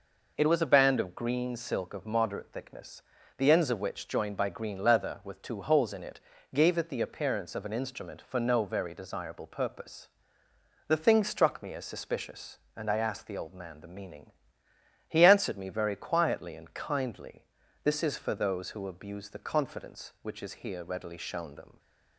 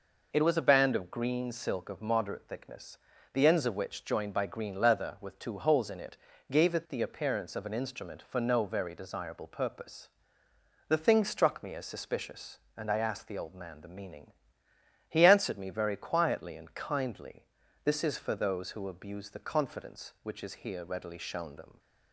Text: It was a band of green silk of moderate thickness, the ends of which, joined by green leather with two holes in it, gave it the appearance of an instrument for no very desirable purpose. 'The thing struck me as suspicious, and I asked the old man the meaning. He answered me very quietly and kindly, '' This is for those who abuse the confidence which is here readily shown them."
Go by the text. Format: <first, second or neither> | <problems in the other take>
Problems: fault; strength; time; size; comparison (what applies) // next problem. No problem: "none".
neither | none